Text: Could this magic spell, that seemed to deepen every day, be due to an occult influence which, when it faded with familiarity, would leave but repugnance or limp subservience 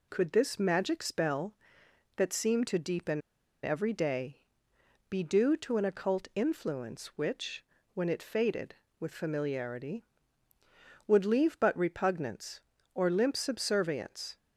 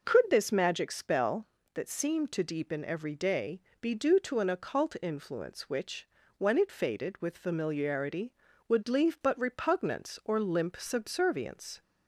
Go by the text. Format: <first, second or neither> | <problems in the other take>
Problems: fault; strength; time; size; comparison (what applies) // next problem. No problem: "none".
second | pauses between "deepen" and "every"; at 3.2 s; 0.42 s long